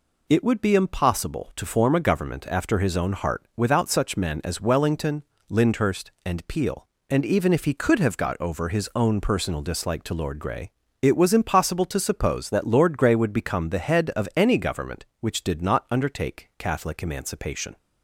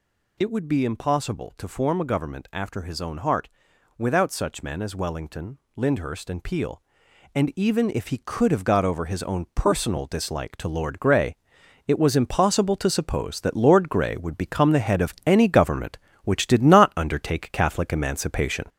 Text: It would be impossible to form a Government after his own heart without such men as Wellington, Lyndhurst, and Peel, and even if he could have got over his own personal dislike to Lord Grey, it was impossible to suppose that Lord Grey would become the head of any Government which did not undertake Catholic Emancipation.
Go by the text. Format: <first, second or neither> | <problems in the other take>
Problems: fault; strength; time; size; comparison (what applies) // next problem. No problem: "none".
first | gets louder; noticeable; throughout; 5 dB // pauses between "heart" and "without"; noticeable; at 3.4 s; 0.48 s long